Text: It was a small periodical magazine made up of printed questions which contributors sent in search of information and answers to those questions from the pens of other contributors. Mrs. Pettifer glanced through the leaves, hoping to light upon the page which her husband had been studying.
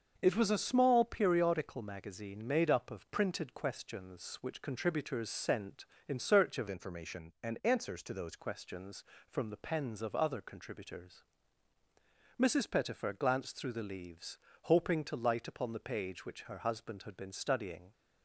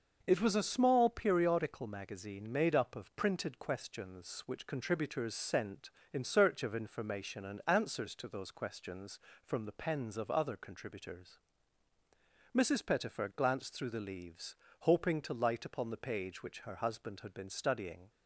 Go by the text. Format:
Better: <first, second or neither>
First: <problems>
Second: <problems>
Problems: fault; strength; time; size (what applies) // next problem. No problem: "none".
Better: second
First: starts louder than the rest; until 1.2 s; 6.5 dB // changes voice from "information" to "those"; from 6.6 to 8.3 s; 1.7 s long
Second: starts louder than the rest; noticeable; until 1.2 s; 6 dB